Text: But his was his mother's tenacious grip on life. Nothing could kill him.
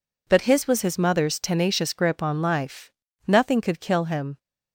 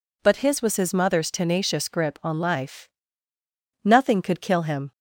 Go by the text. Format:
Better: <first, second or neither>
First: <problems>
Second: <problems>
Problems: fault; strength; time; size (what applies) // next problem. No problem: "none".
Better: neither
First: none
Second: none